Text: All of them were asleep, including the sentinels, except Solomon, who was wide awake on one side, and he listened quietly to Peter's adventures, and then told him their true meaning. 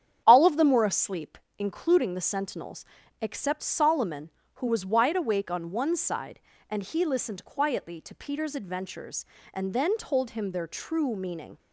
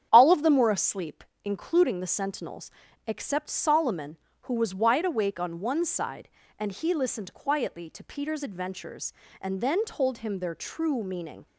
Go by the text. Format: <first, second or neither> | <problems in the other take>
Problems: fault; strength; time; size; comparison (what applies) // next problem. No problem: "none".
neither | starts louder than the rest; strong; the same in both